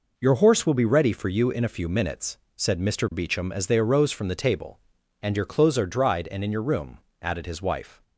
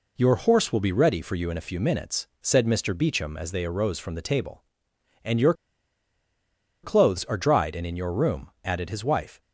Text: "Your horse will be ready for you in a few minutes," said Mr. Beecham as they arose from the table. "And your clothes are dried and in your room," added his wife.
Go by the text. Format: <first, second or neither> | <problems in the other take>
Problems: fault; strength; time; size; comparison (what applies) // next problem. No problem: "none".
first | pauses between "your" and "clothes"; strong; at 5.5 s; 1.3 s long